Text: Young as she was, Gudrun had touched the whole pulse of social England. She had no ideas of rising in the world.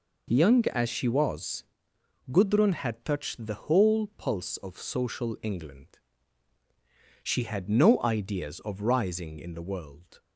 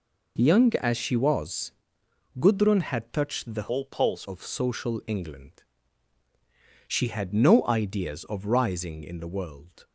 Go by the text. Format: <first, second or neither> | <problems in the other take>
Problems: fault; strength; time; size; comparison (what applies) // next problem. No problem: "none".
first | changes voice from "whole" to "pulse"; from 3.7 to 4.2 s; 0.5 s long